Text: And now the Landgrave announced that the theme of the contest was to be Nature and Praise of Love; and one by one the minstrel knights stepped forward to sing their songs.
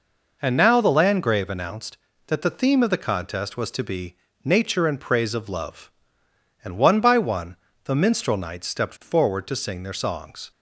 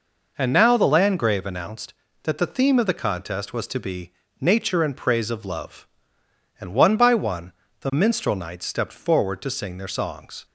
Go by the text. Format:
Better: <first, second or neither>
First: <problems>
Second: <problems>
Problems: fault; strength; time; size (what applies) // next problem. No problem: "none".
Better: neither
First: pauses between "be" and "Nature"; slight; at 4.1 s; 0.28 s long // pauses between "one" and "the"; slight; at 7.5 s; 0.28 s long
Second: pauses between "be" and "Nature"; slight; at 4.1 s; 0.28 s long // pauses between "one" and "the"; slight; at 7.5 s; 0.28 s long